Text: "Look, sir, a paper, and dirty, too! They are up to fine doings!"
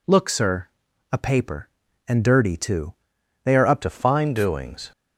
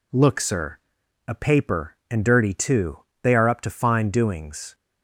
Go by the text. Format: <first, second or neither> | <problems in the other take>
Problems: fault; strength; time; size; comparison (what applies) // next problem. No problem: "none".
second | changes voice at "to"; from 3.8 s on; 1.1 s long